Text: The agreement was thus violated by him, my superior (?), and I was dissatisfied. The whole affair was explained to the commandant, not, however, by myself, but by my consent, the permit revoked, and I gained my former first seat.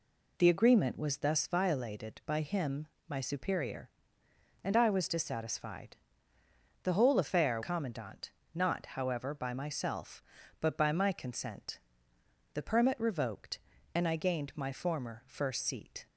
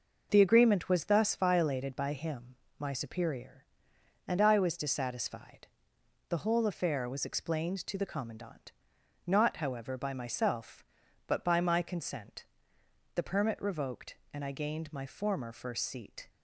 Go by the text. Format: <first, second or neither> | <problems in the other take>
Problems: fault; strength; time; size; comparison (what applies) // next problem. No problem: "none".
second | skips "was explained to the"; at 7.6 s